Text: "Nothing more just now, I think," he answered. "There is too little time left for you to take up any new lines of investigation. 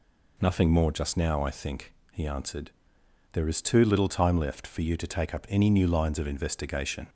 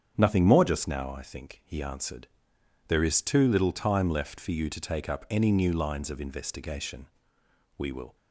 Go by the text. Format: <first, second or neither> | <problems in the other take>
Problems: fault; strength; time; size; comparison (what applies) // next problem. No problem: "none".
first | starts louder than the rest; strong; until 1.1 s; 7.5 dB // goes on to say "We will"; slight; from 7.7 s on; 0.36 s long